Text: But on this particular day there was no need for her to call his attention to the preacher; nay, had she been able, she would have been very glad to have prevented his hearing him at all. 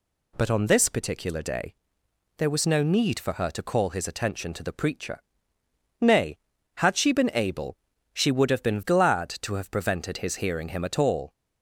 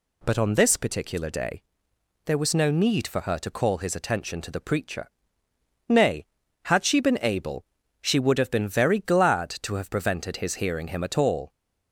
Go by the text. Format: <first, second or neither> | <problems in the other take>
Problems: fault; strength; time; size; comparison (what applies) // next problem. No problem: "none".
second | pauses between "day" and "there"; noticeable; at 1.7 s; 0.64 s long; noticeable in the second // skips "very"; at 8.8 s